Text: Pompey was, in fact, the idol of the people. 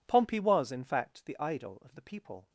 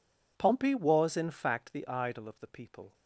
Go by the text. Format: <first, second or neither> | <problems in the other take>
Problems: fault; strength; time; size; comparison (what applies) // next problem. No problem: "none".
neither | none